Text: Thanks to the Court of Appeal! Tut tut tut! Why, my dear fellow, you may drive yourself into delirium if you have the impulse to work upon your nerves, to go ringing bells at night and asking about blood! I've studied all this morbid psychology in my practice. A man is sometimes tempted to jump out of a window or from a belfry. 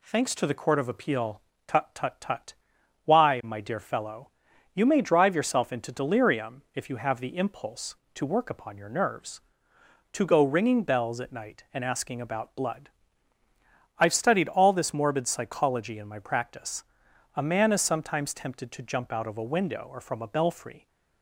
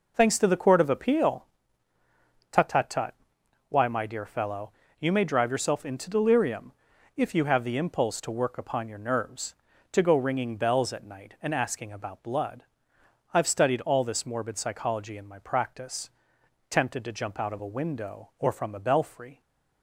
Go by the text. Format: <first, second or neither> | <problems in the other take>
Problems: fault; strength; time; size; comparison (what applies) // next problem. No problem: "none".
first | pauses between "delirium" and "if"; noticeable; at 6.7 s; 0.46 s long // skips "A man is sometimes"; at 16.4 s